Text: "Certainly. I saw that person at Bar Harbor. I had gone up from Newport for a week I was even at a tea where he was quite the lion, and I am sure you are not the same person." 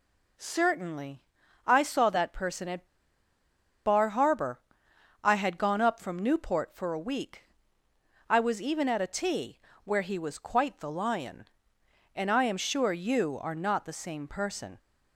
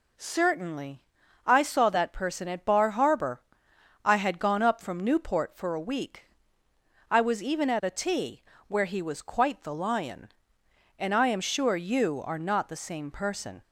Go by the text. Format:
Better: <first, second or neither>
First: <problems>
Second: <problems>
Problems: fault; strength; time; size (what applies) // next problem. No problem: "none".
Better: second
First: pauses between "at" and "Bar"; at 2.8 s; 1.0 s long // pauses between "week" and "I"; noticeable; at 7.4 s; 0.86 s long // pauses between "tea" and "where"; slight; at 9.5 s; 0.24 s long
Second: pauses between "week" and "I"; noticeable; at 6.2 s; 0.86 s long // pauses between "tea" and "where"; slight; at 8.4 s; 0.24 s long